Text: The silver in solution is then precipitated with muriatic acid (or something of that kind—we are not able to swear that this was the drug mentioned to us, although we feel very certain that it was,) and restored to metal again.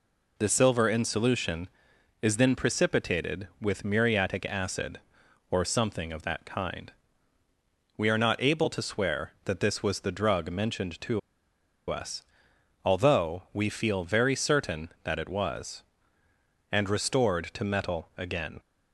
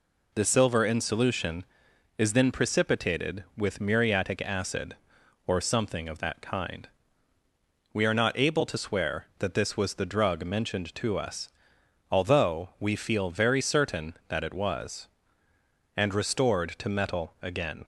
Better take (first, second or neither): second